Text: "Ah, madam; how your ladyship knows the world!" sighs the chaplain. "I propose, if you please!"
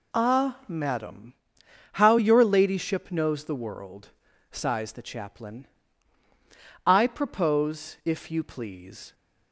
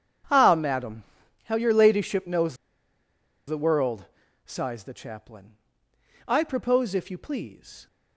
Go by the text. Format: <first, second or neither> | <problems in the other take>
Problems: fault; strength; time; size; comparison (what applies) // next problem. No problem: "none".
first | starts louder than the rest; strong; until 1.7 s; 8.5 dB // pauses between "knows" and "the"; noticeable; at 2.5 s; 0.92 s long